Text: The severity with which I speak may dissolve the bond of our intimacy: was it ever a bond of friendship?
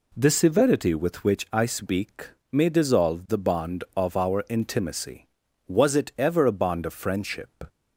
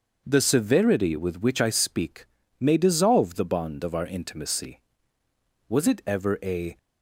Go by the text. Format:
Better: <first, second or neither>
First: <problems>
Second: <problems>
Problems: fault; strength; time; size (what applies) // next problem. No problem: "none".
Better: first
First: pauses between "speak" and "may"; slight; at 2.2 s; 0.22 s long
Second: starts louder than the rest; until 1.2 s; 6 dB // pauses between "speak" and "may"; slight; at 2.2 s; 0.34 s long // stops before "bond of friendship"; at 6.7 s